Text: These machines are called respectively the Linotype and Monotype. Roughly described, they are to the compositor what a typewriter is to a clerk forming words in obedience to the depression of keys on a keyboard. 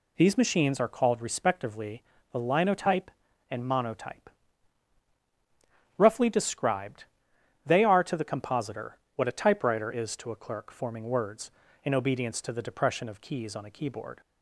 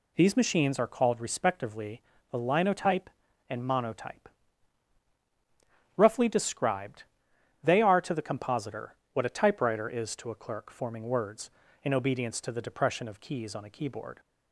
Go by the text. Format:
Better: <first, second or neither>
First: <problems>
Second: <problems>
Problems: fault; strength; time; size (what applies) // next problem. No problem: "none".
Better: neither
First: pauses between "respectively" and "the"; slight; at 2.0 s; 0.30 s long // pauses between "compositor" and "what"; slight; at 8.9 s; 0.18 s long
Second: pauses between "respectively" and "the"; slight; at 2.0 s; 0.30 s long // pauses between "compositor" and "what"; slight; at 8.9 s; 0.18 s long